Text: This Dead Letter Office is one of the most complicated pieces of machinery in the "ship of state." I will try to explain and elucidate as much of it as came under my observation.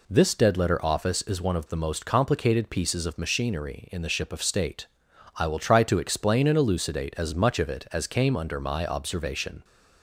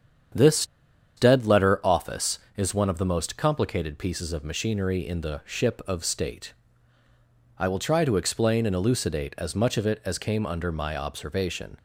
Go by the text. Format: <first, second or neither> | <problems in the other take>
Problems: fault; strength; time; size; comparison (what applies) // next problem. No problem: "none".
first | starts louder than the rest; strong; until 1.8 s; 8 dB // pauses between "This" and "Dead"; noticeable; at 0.6 s; 0.51 s long